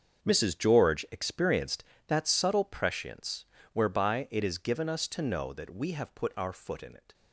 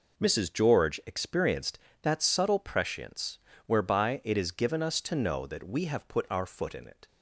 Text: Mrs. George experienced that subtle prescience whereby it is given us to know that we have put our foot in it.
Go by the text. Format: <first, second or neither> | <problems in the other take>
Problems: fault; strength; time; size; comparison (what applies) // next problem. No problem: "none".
second | gets quieter; strong; throughout; 14 dB // pauses between "prescience" and "whereby"; slight; at 3.4 s; 0.28 s long; slight in the second